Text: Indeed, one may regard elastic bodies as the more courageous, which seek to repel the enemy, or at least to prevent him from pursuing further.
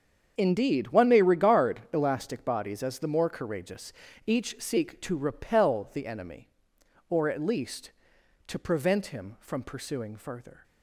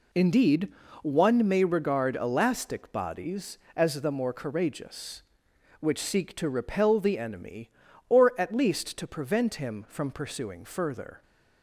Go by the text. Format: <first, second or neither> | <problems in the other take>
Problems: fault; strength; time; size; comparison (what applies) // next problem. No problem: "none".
second | starts louder than the rest; strong; until 1.3 s; 7 dB // says "each" for "which"; at 4.2 s